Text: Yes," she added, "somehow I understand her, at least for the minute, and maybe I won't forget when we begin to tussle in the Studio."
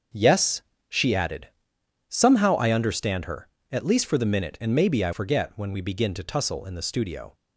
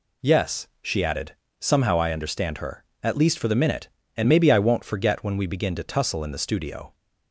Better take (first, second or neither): second